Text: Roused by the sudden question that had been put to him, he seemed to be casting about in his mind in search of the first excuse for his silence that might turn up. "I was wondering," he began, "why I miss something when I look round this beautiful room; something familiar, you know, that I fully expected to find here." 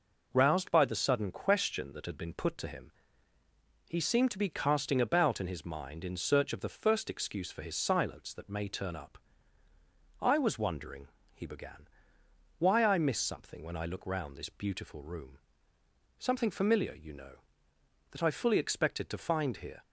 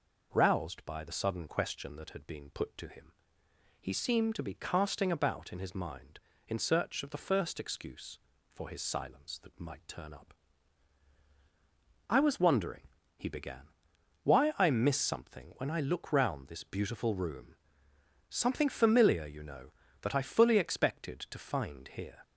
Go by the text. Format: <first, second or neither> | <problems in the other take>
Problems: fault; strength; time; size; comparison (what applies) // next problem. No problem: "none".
second | says "may" for "might"; at 8.4 s